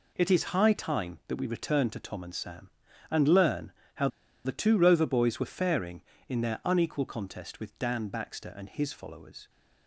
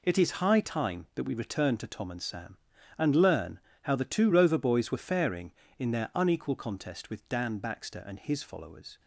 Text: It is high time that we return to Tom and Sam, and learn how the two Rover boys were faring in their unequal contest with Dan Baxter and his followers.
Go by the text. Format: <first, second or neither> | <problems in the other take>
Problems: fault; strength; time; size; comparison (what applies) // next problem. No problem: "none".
second | pauses between "learn" and "how"; slight; at 3.7 s; 0.22 s long; slight in the second // pauses between "how" and "the"; at 4.0 s; 0.36 s long